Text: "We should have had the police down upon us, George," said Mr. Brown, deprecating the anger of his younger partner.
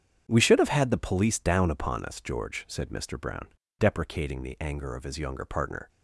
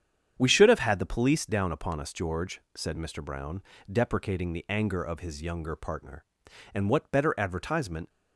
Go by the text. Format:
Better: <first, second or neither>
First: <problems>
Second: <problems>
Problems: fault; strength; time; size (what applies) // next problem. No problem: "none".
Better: first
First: starts louder than the rest; strong; until 1.2 s; 8 dB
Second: starts louder than the rest; strong; until 1.3 s; 8.5 dB // goes on to say "And what better advertisement"; from 6.7 s on; 1.3 s long